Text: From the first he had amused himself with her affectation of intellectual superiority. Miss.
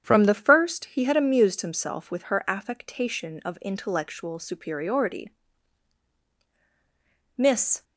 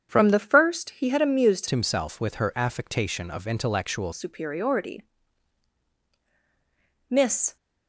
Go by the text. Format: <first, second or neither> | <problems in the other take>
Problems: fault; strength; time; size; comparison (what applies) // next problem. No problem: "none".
first | starts louder than the rest; strong; until 1.1 s; 8 dB; strong in the first // changes voice from "himself" to "intellectual"; from 1.6 to 4.1 s; 2.5 s long